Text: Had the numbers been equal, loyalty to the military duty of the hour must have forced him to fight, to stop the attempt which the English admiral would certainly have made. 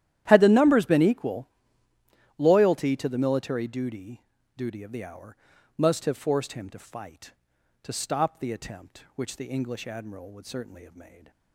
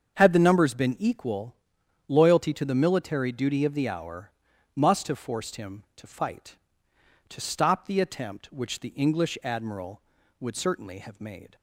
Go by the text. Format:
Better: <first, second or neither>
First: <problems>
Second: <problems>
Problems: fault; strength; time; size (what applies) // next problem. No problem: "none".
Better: second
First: starts louder than the rest; strong; until 1.2 s; 12 dB // says "duty" twice; at 4.5 s // pauses between "hour" and "must"; at 5.3 s; 0.42 s long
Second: starts louder than the rest; strong; until 1.2 s; 7 dB // pauses between "hour" and "must"; noticeable; at 4.2 s; 0.46 s long